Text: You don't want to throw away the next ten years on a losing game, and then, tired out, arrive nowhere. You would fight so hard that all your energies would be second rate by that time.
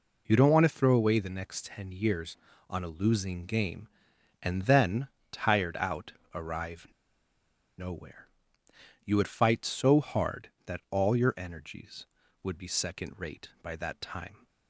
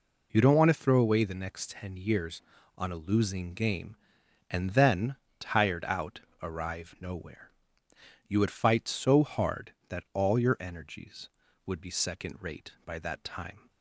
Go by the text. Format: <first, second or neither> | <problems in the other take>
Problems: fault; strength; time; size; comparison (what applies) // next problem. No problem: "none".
second | pauses between "arrive" and "nowhere"; noticeable; at 6.8 s; 0.90 s long